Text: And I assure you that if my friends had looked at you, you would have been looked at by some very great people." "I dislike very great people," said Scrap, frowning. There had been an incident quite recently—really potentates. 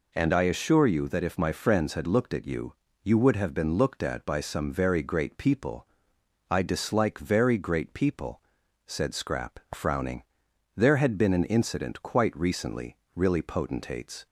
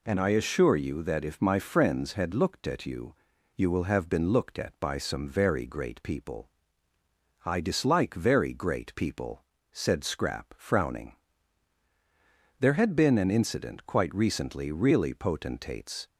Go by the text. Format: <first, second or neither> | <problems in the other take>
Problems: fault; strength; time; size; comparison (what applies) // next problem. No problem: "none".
first | says "will" for "would"; at 3.6 s